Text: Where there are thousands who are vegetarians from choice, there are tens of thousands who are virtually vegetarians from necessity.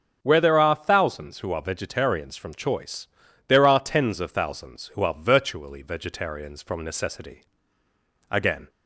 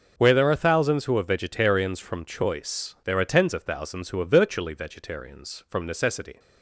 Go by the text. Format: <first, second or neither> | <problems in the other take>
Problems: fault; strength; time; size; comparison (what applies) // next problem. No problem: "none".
second | starts louder than the rest; until 1.2 s; 6.5 dB // goes on to say "Again"; slight; from 8.2 s on; 0.40 s long